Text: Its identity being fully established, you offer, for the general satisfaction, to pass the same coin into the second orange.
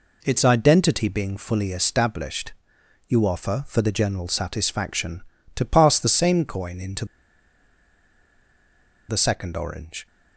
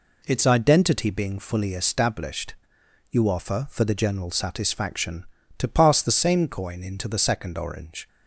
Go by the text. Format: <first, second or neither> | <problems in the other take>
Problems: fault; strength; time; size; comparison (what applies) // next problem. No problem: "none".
second | pauses between "into" and "the"; strong; at 7.0 s; 2.0 s long